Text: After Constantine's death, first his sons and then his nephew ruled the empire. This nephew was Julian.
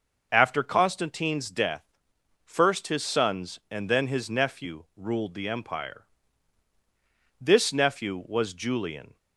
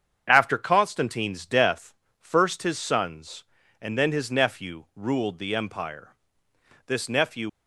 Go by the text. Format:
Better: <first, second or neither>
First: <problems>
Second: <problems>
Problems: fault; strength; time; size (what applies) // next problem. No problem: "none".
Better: first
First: starts louder than the rest; noticeable; until 1.3 s; 6 dB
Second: starts louder than the rest; strong; until 1.2 s; 7.5 dB // stops before "was Julian"; at 7.4 s